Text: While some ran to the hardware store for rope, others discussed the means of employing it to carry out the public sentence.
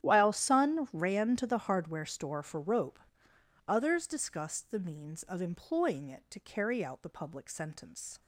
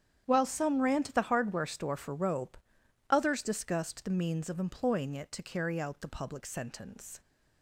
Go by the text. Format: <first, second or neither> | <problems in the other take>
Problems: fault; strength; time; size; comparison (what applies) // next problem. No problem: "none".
second | starts louder than the rest; strong; until 1.0 s; 11 dB; strong in the second // says "sun" for "some"; at 0.3 s